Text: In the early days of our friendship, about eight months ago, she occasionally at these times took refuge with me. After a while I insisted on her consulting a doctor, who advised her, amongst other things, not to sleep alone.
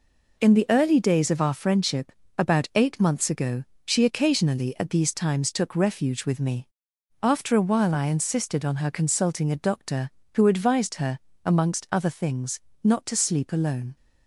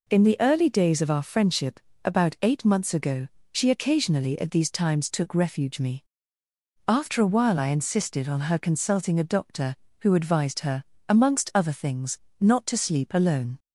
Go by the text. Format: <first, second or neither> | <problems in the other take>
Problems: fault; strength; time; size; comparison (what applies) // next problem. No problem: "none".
first | skips "with"; at 5.8 s